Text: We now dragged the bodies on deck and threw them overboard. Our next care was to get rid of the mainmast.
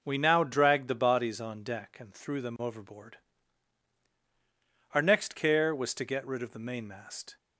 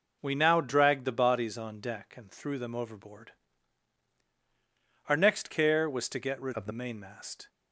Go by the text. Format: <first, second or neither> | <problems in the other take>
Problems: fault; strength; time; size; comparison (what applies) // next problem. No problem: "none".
first | changes voice from "of" to "the"; from 6.5 to 6.7 s; 0.2 s long